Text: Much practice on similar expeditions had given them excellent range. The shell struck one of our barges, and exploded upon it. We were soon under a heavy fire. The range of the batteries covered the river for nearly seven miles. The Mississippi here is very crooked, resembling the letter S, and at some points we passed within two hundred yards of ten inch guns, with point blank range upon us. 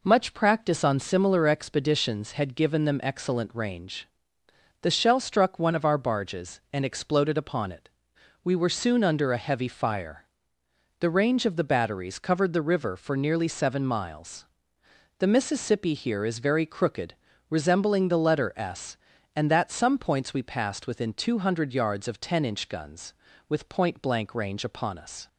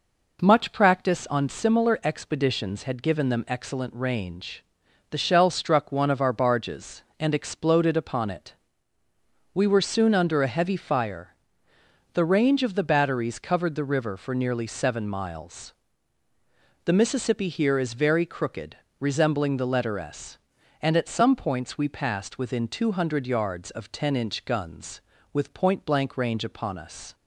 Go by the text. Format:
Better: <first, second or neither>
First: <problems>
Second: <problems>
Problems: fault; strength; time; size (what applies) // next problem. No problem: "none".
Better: second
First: says "that" for "at"; at 19.5 s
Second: none